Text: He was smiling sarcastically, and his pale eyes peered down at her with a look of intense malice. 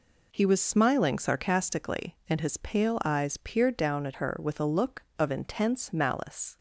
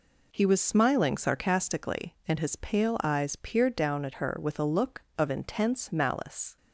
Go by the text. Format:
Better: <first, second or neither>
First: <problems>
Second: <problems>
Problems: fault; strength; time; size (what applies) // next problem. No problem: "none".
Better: neither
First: none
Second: none